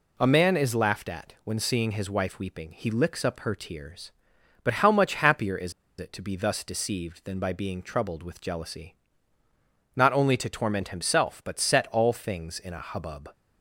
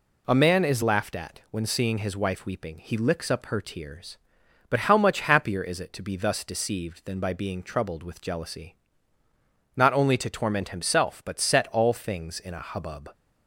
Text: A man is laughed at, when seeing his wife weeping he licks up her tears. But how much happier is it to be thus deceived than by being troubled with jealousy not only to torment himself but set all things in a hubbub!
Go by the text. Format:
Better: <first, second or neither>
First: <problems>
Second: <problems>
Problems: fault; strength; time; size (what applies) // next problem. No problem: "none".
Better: second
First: pauses between "is" and "it"; slight; at 5.7 s; 0.27 s long // pauses between "jealousy" and "not"; at 8.9 s; 1.0 s long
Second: pauses between "jealousy" and "not"; at 8.7 s; 1.0 s long